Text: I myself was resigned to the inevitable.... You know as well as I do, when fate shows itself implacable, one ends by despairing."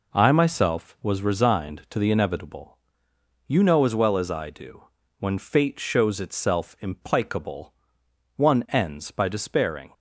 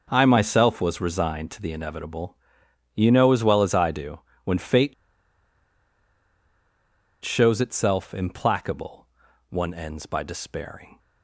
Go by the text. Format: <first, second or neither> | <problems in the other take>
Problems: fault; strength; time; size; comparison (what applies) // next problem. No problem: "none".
first | pauses between "fate" and "shows"; strong; at 4.9 s; 2.3 s long